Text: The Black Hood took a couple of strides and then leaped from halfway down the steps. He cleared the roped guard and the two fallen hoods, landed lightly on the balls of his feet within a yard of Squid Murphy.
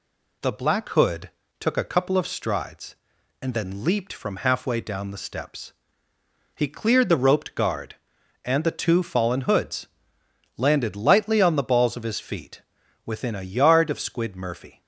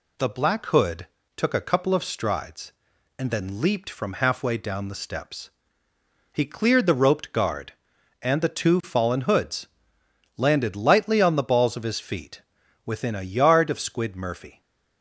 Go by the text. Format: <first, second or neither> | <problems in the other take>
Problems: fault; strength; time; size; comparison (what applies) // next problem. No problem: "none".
neither | pauses between "Hood" and "took"; slight; the same in both // pauses between "feet" and "within"; the same in both